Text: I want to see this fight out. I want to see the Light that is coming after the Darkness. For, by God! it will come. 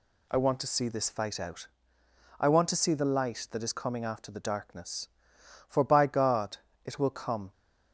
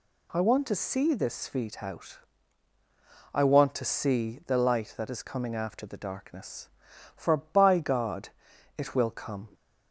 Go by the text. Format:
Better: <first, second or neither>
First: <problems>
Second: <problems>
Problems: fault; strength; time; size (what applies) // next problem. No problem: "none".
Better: first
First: none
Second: says "feet" for "fight"; at 1.4 s